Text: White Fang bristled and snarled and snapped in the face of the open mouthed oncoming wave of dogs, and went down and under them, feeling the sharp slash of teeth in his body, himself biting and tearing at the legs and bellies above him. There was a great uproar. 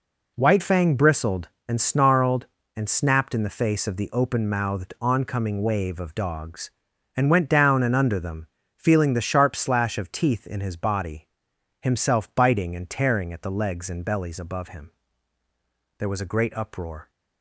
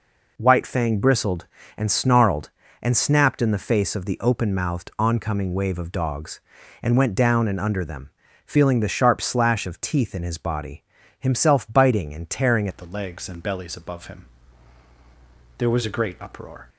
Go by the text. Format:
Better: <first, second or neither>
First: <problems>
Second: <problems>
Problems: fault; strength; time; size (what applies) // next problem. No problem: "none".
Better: first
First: none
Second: changes voice at "at"; from 12.6 s on; 4.0 s long